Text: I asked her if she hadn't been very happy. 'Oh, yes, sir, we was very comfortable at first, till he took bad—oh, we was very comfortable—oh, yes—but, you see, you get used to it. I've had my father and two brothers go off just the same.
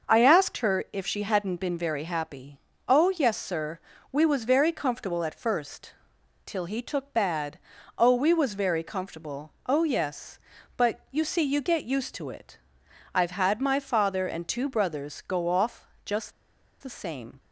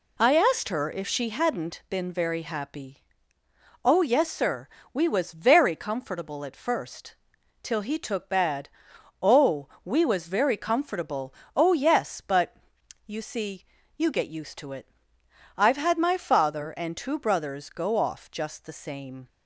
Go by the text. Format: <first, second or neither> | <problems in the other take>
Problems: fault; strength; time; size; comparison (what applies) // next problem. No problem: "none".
second | starts louder than the rest; noticeable; until 1.1 s; 6 dB // pauses between "off" and "just"; slight; at 15.8 s; 0.16 s long // pauses between "just" and "the"; noticeable; at 16.3 s; 0.50 s long